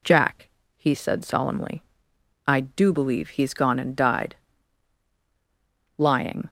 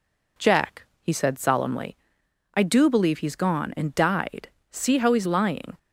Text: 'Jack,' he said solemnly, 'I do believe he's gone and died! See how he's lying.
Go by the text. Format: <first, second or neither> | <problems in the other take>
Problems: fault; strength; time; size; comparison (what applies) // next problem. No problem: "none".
second | skips "See how he's"; at 5.1 s